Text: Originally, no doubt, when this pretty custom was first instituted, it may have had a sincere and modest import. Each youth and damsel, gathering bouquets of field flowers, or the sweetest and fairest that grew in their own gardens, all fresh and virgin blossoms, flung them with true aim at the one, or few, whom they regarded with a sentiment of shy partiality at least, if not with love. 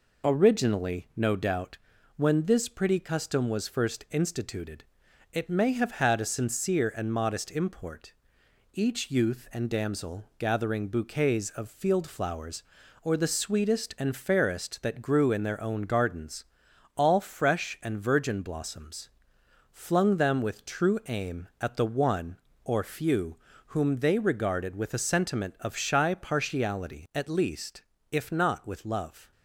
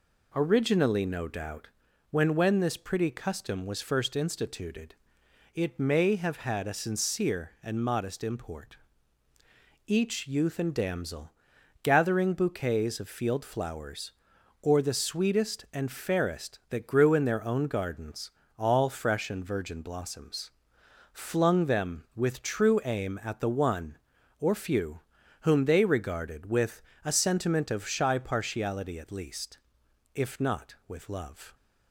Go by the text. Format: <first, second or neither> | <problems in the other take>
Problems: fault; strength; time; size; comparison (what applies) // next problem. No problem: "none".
first | says "when" twice; at 2.3 s // pauses between "with" and "a"; slight; at 26.8 s; 0.24 s long